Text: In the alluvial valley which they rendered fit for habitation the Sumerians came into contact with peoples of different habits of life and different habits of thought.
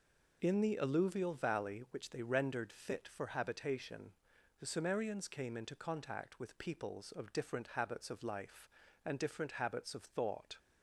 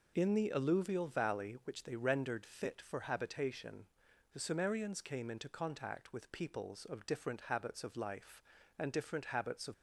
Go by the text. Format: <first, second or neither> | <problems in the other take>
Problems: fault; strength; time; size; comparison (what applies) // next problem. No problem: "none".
first | pauses between "habitation" and "the"; at 3.8 s; 0.44 s long; also in the first // stops before "thought"; at 9.7 s